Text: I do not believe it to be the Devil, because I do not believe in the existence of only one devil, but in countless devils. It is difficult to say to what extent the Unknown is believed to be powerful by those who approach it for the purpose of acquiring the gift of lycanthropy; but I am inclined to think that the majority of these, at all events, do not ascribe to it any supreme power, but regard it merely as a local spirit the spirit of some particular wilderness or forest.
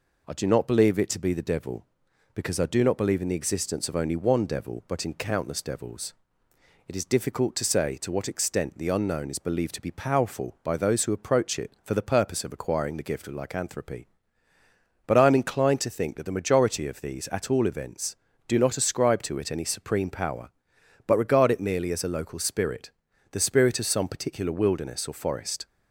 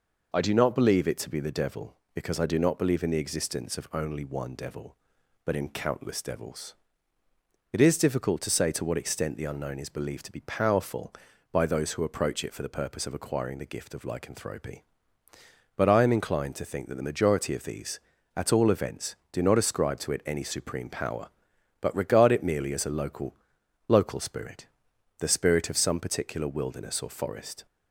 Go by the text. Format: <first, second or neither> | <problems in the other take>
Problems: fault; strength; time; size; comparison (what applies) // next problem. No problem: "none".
first | says "local" twice; at 23.8 s // pauses between "spirit" and "the"; noticeable; at 24.6 s; 0.52 s long; also in the first